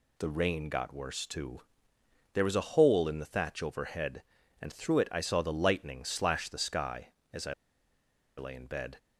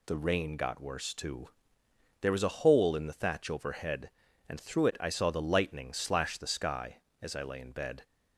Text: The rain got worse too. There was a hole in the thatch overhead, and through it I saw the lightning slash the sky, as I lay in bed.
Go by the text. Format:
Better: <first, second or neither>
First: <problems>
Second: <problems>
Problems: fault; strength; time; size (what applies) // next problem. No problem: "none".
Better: second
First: pauses between "I" and "lay"; noticeable; at 7.5 s; 0.84 s long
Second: none